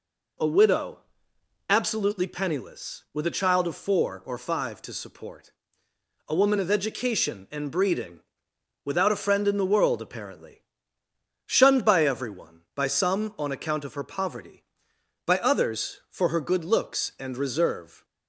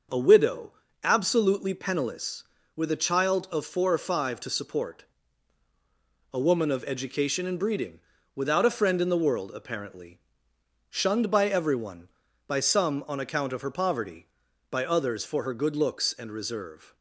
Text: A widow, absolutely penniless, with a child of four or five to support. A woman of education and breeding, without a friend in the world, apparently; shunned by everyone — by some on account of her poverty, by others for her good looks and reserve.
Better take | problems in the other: neither | none

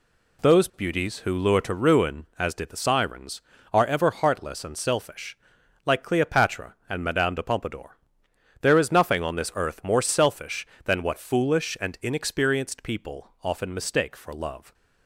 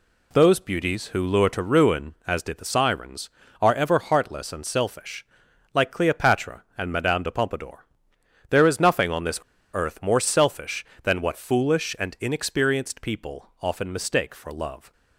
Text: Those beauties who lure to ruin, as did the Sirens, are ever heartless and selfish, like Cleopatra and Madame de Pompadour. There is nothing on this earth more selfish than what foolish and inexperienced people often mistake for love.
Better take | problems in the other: first | pauses between "this" and "earth"; slight; at 9.4 s; 0.32 s long

